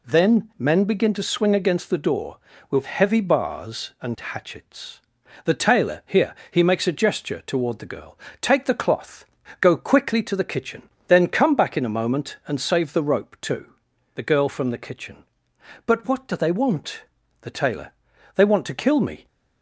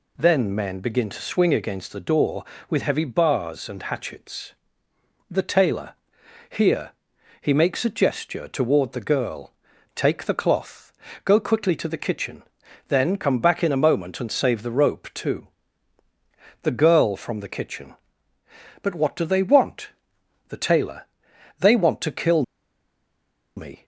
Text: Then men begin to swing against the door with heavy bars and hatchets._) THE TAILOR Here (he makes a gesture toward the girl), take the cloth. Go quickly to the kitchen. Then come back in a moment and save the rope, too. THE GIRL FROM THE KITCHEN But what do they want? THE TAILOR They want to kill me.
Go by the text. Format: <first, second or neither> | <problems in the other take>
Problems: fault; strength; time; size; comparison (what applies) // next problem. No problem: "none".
first | pauses between "TAILOR" and "Here"; noticeable; at 5.9 s; 0.56 s long // pauses between "TAILOR" and "They"; noticeable; at 21.0 s; 0.54 s long; also in the first // pauses between "kill" and "me"; at 22.4 s; 1.1 s long